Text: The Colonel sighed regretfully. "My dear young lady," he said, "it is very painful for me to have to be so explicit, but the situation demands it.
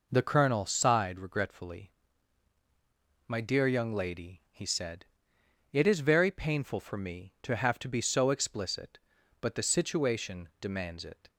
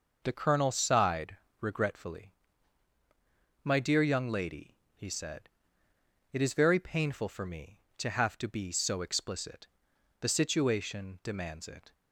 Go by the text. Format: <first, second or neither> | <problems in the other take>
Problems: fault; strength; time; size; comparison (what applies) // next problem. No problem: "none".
first | pauses between "sighed" and "regretfully"; slight; at 1.3 s; 0.24 s long // skips "but"; at 9.9 s